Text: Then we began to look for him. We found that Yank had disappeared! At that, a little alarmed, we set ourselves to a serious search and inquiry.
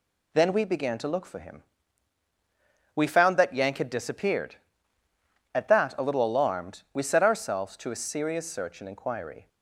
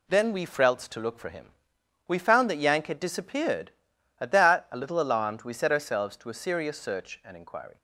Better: first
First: none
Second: says "frelts" for "began"; at 0.4 s

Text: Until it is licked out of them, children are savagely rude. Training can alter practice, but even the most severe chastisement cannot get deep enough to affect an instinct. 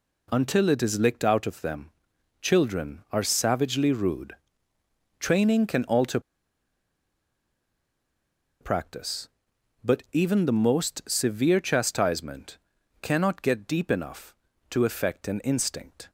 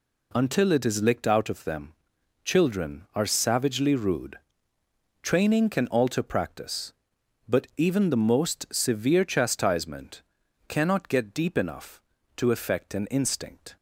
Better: second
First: pauses between "alter" and "practice"; strong; at 6.1 s; 2.4 s long // pauses between "chastisement" and "cannot"; at 12.5 s; 0.42 s long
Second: pauses between "chastisement" and "cannot"; at 10.2 s; 0.44 s long

